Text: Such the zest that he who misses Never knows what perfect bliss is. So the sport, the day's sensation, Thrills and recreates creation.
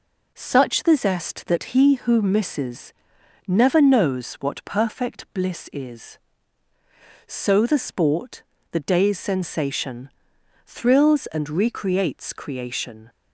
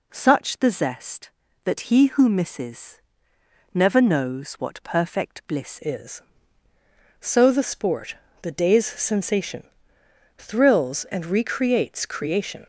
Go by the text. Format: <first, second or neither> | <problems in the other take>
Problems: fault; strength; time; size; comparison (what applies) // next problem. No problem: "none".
first | pauses between "misses" and "Never"; noticeable; at 2.9 s; 0.74 s long; noticeable in the first // changes voice at "is"; from 5.8 s on; 6.8 s long